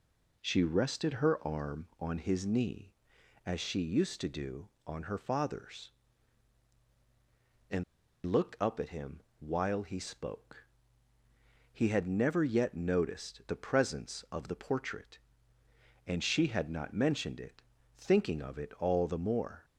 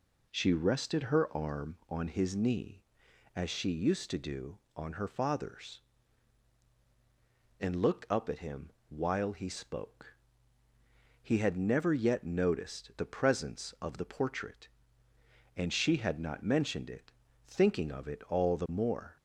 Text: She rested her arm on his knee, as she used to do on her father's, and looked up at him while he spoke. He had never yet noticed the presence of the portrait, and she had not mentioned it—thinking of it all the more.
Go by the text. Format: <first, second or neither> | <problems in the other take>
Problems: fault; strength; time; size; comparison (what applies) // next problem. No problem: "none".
second | pauses between "and" and "looked"; at 7.8 s; 0.40 s long // pauses between "him" and "while"; slight; at 9.2 s; 0.20 s long; slight in the second